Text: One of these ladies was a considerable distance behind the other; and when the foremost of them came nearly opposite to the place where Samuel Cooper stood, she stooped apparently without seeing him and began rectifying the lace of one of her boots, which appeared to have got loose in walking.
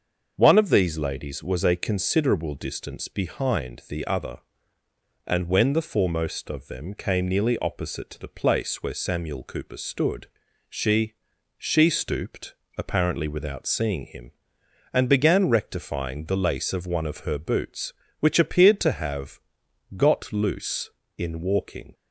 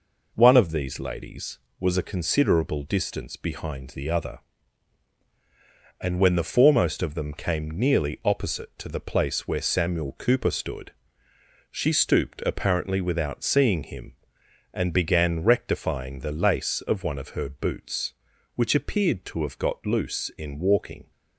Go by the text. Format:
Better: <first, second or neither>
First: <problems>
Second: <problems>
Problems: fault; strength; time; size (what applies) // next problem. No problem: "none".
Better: second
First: starts louder than the rest; until 1.3 s; 6.5 dB // says "she" twice; at 11.5 s // pauses between "stooped" and "apparently"; slight; at 12.5 s; 0.24 s long // pauses between "have" and "got"; noticeable; at 19.3 s; 0.56 s long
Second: none